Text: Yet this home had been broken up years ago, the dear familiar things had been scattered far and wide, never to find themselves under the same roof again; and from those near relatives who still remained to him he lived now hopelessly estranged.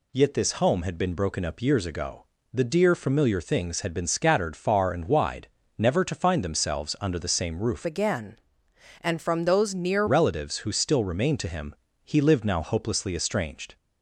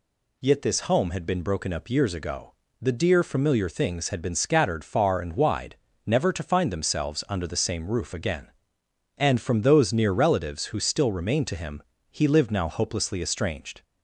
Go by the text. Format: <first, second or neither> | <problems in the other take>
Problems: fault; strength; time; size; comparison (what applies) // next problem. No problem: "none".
second | changes voice from "again" to "near"; from 7.8 to 10.0 s; 2.2 s long // pauses between "him" and "he"; slight; at 11.7 s; 0.26 s long; slight in the second